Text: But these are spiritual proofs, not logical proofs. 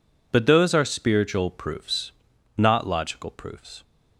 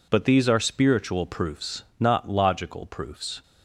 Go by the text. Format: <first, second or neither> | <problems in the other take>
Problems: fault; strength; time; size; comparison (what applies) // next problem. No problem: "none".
second | says "those" for "these"; at 0.4 s